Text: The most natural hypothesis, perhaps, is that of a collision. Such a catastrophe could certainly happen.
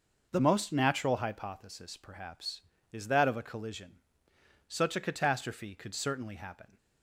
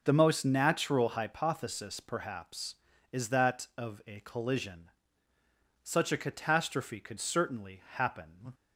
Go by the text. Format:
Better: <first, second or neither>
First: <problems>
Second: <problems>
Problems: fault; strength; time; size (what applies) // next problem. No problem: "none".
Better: neither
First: none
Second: none